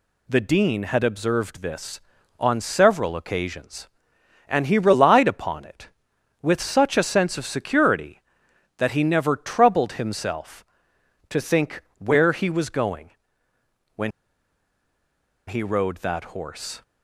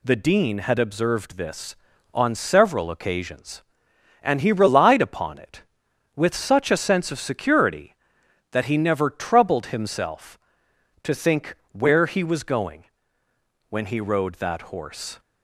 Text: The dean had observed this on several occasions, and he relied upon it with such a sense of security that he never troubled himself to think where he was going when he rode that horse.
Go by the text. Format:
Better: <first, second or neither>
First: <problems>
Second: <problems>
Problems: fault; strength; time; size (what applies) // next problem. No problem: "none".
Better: second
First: pauses between "think" and "where"; slight; at 11.8 s; 0.16 s long // pauses between "going" and "when"; noticeable; at 13.0 s; 0.86 s long // pauses between "when" and "he"; strong; at 14.1 s; 1.3 s long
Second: pauses between "think" and "where"; slight; at 11.5 s; 0.16 s long // pauses between "going" and "when"; noticeable; at 12.8 s; 0.86 s long